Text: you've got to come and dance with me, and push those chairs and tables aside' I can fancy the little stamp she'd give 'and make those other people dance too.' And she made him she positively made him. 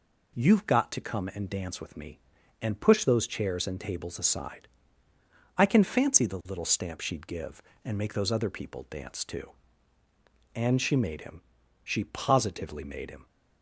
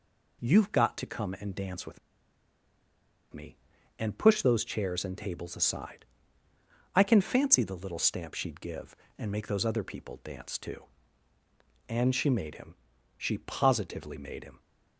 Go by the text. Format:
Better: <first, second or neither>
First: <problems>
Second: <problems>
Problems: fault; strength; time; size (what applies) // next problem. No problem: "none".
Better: first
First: pauses between "aside" and "I"; noticeable; at 4.6 s; 0.88 s long // pauses between "him" and "she"; at 11.3 s; 0.42 s long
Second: pauses between "with" and "me"; strong; at 1.9 s; 1.3 s long // pauses between "aside" and "I"; noticeable; at 6.0 s; 0.88 s long // pauses between "him" and "she"; at 12.7 s; 0.42 s long